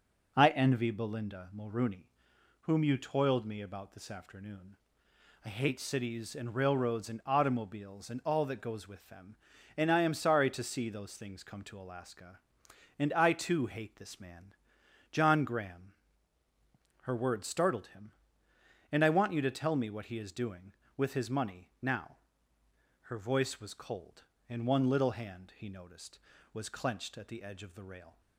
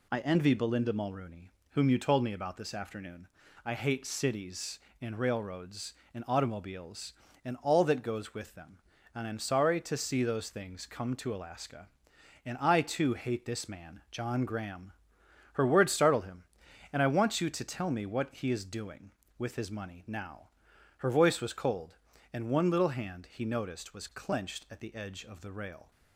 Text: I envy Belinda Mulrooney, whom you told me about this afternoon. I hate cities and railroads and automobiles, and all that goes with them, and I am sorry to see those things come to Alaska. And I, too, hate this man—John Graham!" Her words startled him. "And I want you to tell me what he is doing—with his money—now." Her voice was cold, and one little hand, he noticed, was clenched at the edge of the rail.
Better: second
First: says "toiled" for "told"; at 2.9 s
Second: none

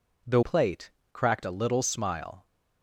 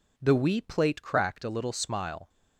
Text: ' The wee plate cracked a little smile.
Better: second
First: skips "wee"; at 0.4 s // pauses between "plate" and "cracked"; slight; at 0.9 s; 0.20 s long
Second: none

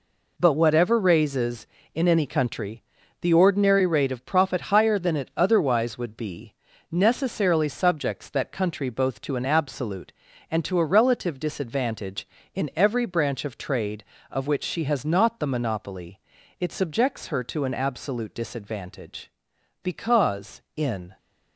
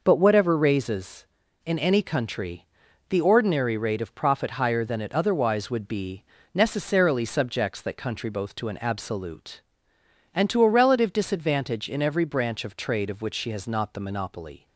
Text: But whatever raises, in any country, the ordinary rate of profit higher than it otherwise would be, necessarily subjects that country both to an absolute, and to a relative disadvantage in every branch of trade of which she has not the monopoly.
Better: second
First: goes on to say "It subjects her to an absolute disadvantage because in"; strong; from 16.5 s on; 4.5 s long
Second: none

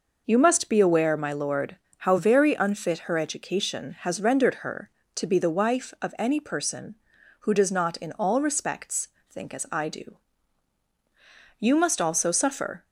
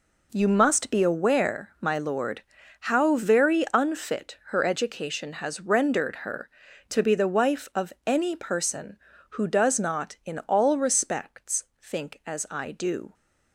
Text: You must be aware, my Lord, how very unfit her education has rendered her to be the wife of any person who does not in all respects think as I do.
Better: second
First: pauses between "respects" and "think"; slight; at 9.0 s; 0.22 s long // goes on to say "You must also suffer"; noticeable; from 11.6 s on; 1.2 s long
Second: pauses between "respects" and "think"; slight; at 11.6 s; 0.18 s long

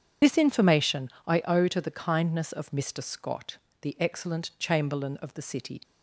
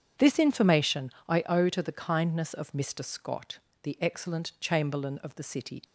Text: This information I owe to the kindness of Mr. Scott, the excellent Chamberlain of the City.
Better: second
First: loses the start of "This"; at 0.2 s; 55 ms // starts louder than the rest; strong; until 1.4 s; 8 dB // pauses between "information" and "I"; slight; at 1.0 s; 0.18 s long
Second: starts louder than the rest; strong; until 1.3 s; 8.5 dB // pauses between "information" and "I"; slight; at 1.1 s; 0.18 s long

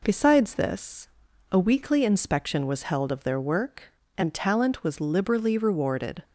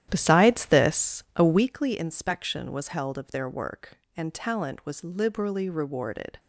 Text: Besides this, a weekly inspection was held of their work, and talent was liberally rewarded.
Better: first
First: none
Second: starts louder than the rest; strong; until 1.7 s; 11.5 dB

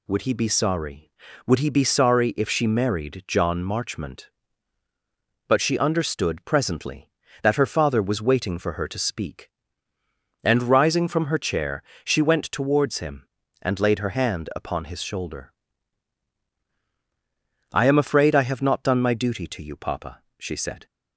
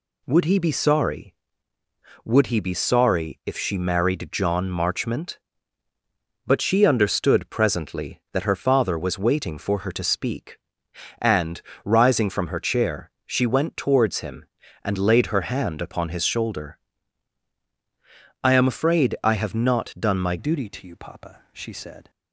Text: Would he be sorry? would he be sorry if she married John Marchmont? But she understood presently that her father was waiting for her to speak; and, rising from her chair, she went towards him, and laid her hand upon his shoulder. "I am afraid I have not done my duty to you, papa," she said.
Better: first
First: none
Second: changes voice at "duty"; from 20.3 s on; 1.7 s long

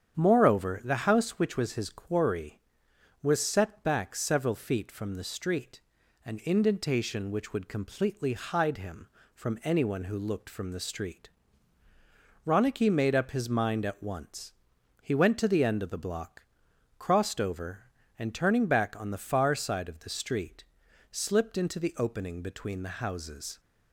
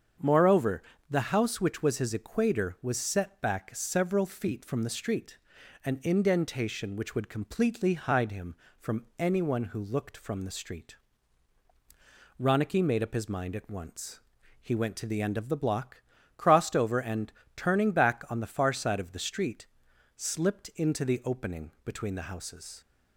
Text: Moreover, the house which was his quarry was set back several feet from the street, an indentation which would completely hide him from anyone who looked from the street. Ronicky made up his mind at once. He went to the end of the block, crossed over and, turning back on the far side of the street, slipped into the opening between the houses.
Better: first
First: starts louder than the rest; strong; until 1.1 s; 8.5 dB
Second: starts louder than the rest; strong; until 1.4 s; 7 dB // says "equator" for "quarry"; at 2.1 s

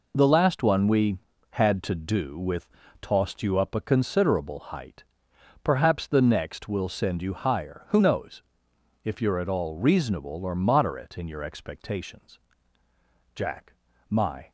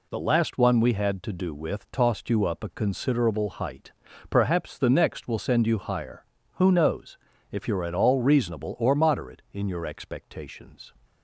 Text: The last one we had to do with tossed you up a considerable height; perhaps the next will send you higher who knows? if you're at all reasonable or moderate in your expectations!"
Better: second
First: pauses between "with" and "tossed"; slight; at 2.6 s; 0.32 s long // goes on to say "Jack my"; noticeable; from 13.3 s on; 1.1 s long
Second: none

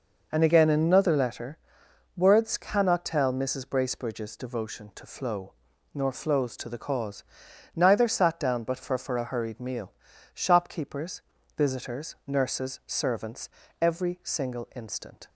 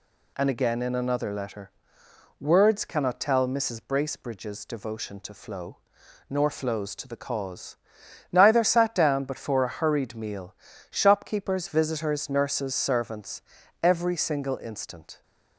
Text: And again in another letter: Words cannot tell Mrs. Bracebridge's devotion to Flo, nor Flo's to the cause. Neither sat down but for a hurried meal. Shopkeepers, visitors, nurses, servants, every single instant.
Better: second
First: says "for" twice; at 8.9 s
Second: none

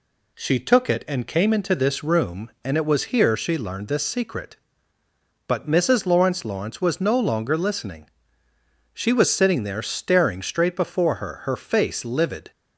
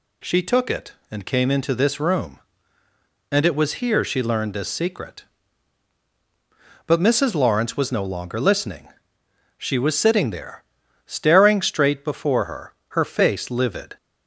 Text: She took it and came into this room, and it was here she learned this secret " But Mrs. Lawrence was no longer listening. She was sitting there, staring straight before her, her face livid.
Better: second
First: says "Lawrence" twice; at 6.4 s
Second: none

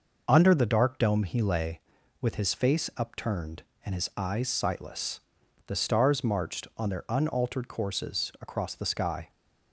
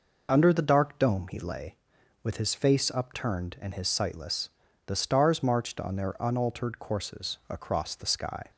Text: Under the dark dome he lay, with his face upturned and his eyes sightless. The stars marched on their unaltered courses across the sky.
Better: first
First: none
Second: skips "eyes"; at 3.8 s

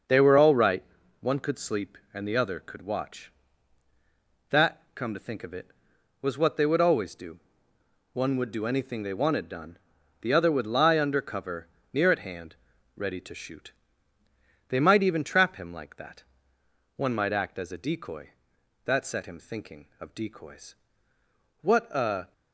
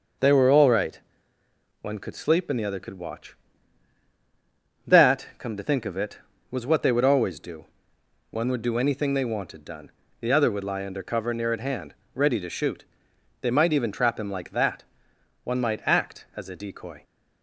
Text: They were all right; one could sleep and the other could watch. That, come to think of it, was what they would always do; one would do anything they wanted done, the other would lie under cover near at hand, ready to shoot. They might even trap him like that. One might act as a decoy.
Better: second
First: starts louder than the rest; until 1.4 s; 6 dB // pauses between "cover" and "near"; slight; at 11.6 s; 0.24 s long // goes on to say "That set him thinking of decoys What a"; strong; from 18.8 s on; 3.4 s long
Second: none

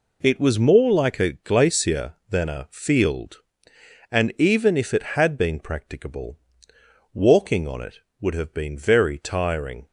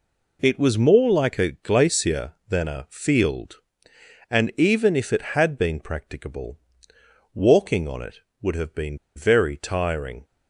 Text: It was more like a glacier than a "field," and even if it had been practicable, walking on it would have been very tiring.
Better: first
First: none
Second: pauses between "been" and "very"; slight; at 8.9 s; 0.18 s long

